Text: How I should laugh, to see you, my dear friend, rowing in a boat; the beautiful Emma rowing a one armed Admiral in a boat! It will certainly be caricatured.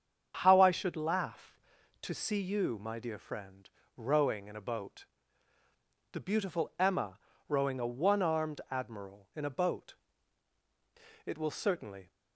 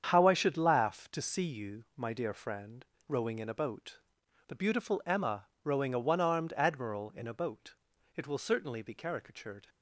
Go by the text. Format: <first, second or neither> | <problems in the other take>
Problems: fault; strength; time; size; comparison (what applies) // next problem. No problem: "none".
second | starts louder than the rest; strong; until 1.4 s; 8 dB; strong in the second // pauses between "Emma" and "rowing"; slight; at 7.1 s; 0.30 s long; slight in the second // stops before "be caricatured"; at 12.0 s